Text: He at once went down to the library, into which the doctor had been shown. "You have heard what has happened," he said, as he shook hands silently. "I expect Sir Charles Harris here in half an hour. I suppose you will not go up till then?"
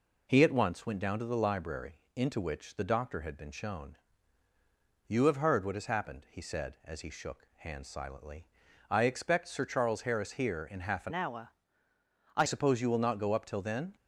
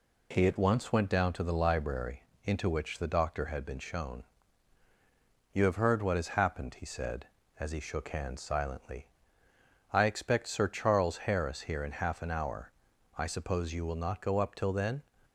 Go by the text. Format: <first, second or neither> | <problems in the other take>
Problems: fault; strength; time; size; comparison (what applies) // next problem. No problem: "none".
second | changes voice from "hour" to "I"; from 11.1 to 12.4 s; 1.3 s long